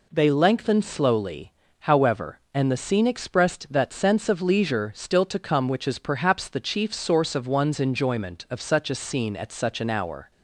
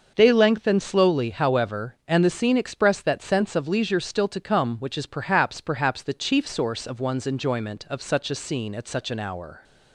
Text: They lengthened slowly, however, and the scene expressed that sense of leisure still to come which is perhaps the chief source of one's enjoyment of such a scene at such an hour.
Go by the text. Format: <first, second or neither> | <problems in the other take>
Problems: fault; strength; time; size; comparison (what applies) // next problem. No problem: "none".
first | starts louder than the rest; noticeable; until 1.1 s; 6 dB // says "perhaps" twice; at 5.5 s